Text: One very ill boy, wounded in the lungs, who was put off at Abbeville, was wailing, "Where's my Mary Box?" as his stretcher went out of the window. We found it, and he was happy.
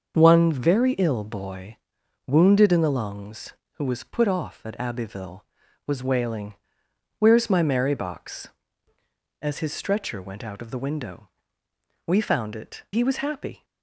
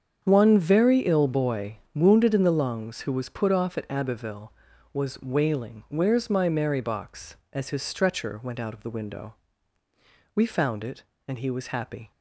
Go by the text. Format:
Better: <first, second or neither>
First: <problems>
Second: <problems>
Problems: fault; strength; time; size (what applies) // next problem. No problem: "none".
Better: second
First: starts louder than the rest; until 1.1 s; 6.5 dB // skips "and"; at 12.8 s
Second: starts louder than the rest; strong; until 1.2 s; 7.5 dB